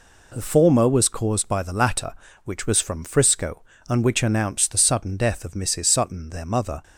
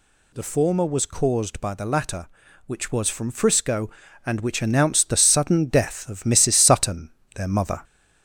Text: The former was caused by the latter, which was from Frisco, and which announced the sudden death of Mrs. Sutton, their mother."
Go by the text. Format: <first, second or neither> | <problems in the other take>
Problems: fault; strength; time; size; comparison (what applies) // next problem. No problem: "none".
first | gets louder; slight; throughout; 2.5 dB